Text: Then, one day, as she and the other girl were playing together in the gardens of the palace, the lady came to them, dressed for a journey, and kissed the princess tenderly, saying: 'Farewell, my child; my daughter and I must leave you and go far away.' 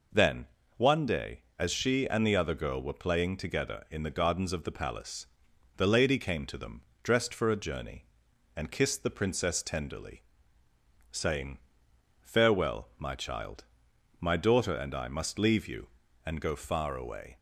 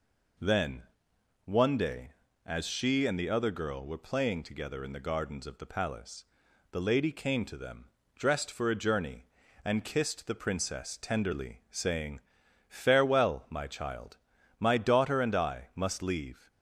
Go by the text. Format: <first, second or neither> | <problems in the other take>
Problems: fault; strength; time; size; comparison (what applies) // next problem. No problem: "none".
first | stops before "you and go far away"; at 16.5 s